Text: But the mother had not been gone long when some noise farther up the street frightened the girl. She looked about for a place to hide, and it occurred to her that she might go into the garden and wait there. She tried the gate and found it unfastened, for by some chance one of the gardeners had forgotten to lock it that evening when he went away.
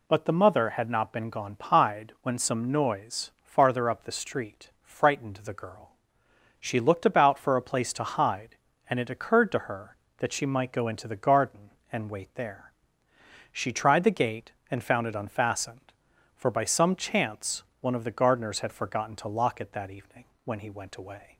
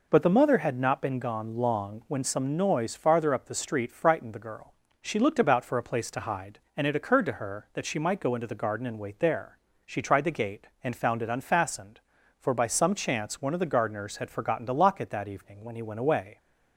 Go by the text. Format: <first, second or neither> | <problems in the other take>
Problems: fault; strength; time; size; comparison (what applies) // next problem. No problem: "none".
second | says "pied" for "long"; at 1.5 s // pauses between "chance" and "one"; slight; at 17.6 s; 0.18 s long // pauses between "evening" and "when"; slight; at 20.2 s; 0.18 s long